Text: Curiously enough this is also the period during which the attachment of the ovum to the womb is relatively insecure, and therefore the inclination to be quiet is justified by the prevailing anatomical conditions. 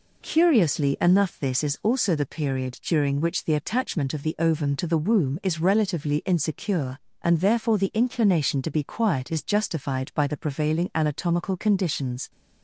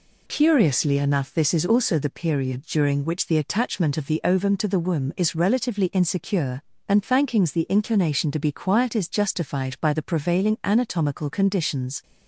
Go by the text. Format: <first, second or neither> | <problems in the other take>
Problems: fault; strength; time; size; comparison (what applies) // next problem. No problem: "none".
first | says "thankings" for "therefore"; at 7.0 s